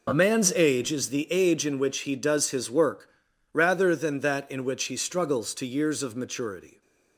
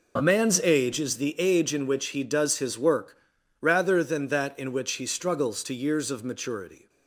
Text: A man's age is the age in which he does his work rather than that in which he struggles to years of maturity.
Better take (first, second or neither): neither